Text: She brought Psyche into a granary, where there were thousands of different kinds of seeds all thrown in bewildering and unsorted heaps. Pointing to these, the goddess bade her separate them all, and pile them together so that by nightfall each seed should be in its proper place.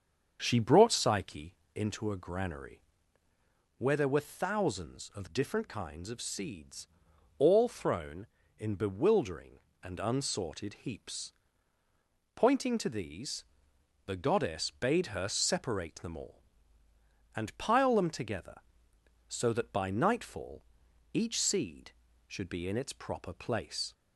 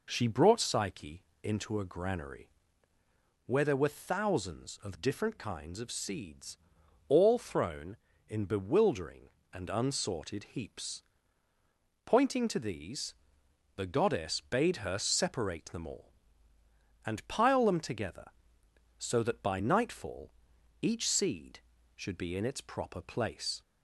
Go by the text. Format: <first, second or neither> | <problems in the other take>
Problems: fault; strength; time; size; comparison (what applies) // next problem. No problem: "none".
second | starts louder than the rest; strong; until 1.6 s; 7 dB // pauses between "Psyche" and "into"; slight; at 1.5 s; 0.22 s long; slight in the second // pauses between "seeds" and "all"; noticeable; at 6.8 s; 0.52 s long; noticeable in the second // pauses between "nightfall" and "each"; noticeable; at 20.6 s; 0.50 s long; noticeable in the second